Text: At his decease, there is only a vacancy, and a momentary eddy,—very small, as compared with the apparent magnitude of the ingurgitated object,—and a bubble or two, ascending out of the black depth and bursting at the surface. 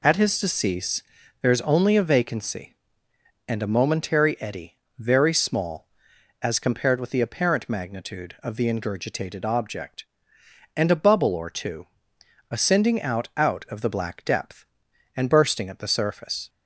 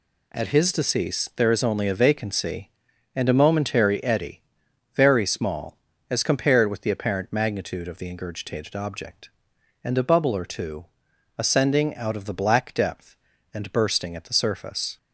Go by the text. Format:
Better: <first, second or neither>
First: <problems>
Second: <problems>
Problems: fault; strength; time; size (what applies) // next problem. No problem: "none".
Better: second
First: says "out" twice; at 13.3 s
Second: none